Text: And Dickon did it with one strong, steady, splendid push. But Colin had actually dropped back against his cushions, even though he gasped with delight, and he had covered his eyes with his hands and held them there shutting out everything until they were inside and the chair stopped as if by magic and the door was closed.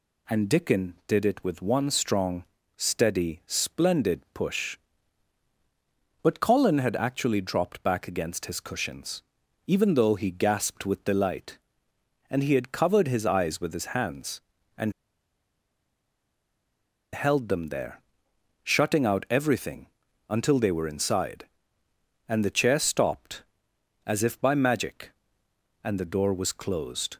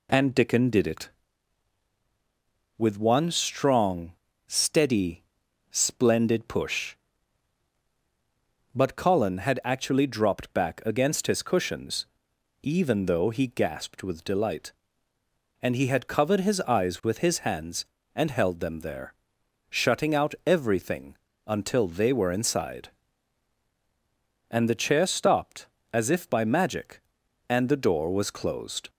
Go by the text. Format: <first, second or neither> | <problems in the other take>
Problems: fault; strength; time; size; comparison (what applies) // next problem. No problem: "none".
second | pauses between "and" and "held"; strong; at 14.9 s; 2.2 s long // pauses between "there" and "shutting"; noticeable; at 17.9 s; 0.66 s long; noticeable in the second // pauses between "everything" and "until"; at 19.8 s; 0.42 s long; slight in the second